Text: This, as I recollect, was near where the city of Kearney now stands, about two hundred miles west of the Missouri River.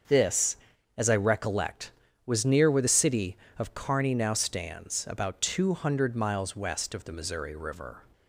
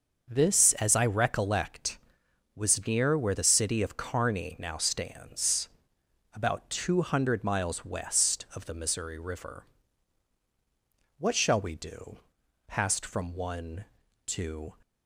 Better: first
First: starts louder than the rest; until 1.4 s; 6.5 dB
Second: starts louder than the rest; until 1.3 s; 6.5 dB // goes on to say "What shall we do passed from one to"; strong; from 11.1 s on; 3.5 s long

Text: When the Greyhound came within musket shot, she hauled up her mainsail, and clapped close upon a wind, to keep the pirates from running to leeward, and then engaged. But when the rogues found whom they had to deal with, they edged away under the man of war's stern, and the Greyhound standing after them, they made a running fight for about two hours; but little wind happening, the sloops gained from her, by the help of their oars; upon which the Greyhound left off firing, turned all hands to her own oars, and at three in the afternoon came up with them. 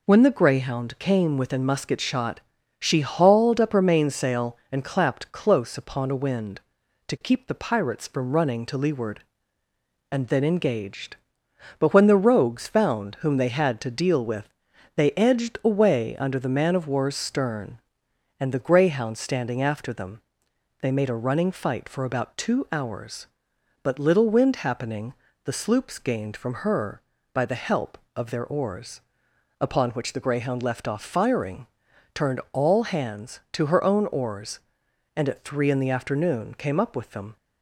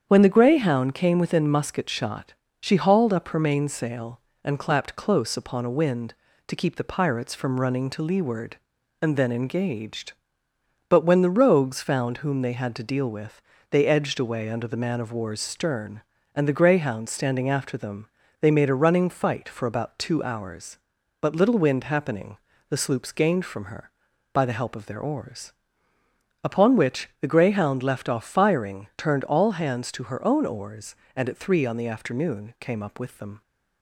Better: first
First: none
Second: starts louder than the rest; strong; until 1.0 s; 8 dB // says "on" for "in"; at 31.6 s

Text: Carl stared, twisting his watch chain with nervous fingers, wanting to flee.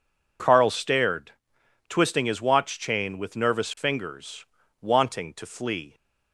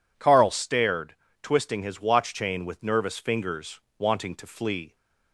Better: neither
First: none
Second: none

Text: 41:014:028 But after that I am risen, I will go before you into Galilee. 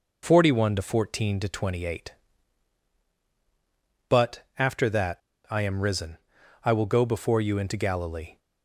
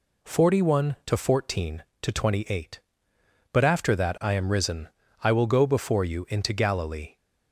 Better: second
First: pauses between "But" and "after"; slight; at 4.4 s; 0.16 s long // pauses between "that" and "I"; slight; at 5.1 s; 0.30 s long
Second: none

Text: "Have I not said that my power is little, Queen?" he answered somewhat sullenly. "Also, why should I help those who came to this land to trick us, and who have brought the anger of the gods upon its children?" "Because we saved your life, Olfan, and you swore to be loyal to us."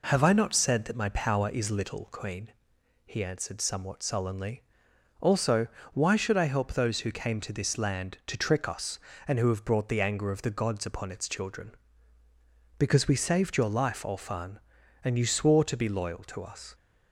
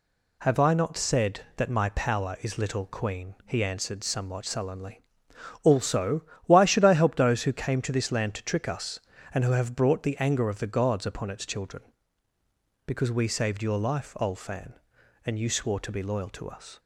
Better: neither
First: none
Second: none

